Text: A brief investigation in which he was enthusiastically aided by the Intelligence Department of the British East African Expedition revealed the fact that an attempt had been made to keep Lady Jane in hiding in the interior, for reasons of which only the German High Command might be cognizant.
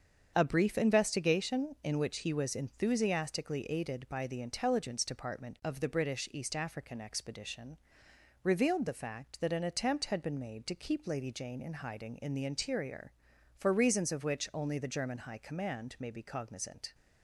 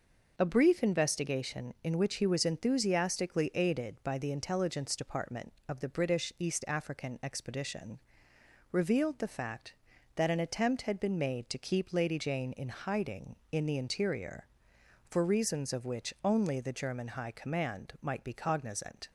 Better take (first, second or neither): second